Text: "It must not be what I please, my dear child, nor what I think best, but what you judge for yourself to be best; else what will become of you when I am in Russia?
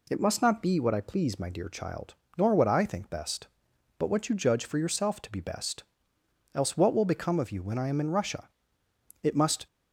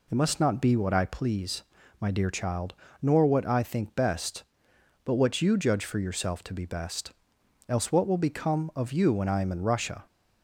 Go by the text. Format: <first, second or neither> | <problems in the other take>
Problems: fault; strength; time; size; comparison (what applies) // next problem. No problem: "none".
second | goes on to say "It must"; slight; from 9.2 s on; 0.44 s long